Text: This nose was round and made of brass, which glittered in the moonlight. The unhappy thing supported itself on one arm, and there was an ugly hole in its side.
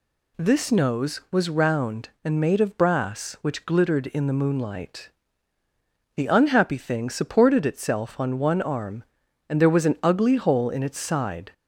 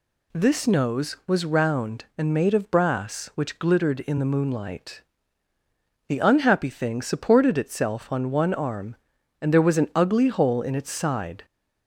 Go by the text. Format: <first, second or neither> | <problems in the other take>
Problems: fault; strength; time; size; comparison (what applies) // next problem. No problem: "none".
neither | none